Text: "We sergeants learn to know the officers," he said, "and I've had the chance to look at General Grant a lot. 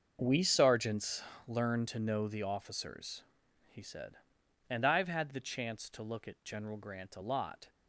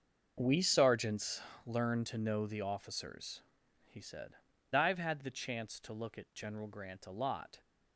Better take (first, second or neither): first